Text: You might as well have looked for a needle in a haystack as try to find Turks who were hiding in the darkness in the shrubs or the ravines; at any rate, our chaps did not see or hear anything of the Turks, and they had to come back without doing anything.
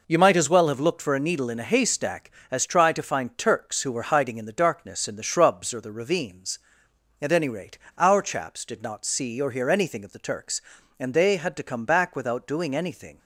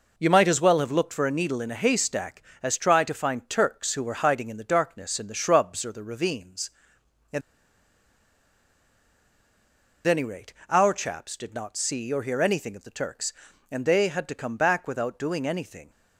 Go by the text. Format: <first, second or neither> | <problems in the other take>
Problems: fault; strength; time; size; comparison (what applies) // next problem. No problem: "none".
first | pauses between "at" and "any"; strong; at 7.4 s; 2.6 s long